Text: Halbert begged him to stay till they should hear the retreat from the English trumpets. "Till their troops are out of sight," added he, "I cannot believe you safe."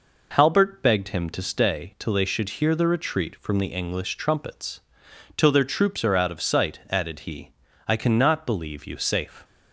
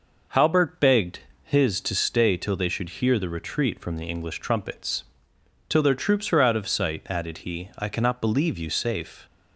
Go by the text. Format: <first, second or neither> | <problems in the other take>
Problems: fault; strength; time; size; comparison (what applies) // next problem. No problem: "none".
first | says "his" for "him"; at 1.4 s